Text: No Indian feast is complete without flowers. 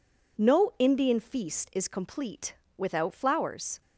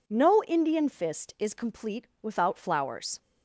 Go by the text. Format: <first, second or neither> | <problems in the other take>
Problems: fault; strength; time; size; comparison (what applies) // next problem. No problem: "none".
first | says "fist" for "feast"; at 0.8 s // pauses between "complete" and "without"; slight; at 2.0 s; 0.16 s long; slight in the first